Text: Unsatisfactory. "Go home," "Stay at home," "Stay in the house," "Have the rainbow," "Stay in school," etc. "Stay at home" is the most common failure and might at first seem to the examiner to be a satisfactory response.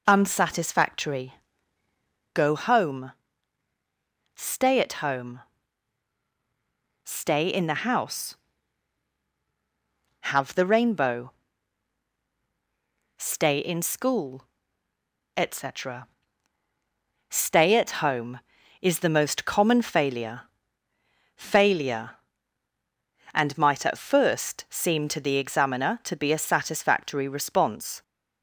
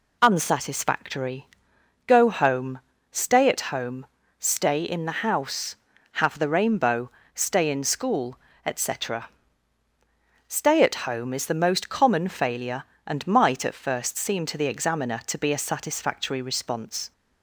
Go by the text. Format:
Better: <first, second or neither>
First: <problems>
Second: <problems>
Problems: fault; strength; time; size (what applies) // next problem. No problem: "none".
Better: second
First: says "failure" twice; at 21.3 s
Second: none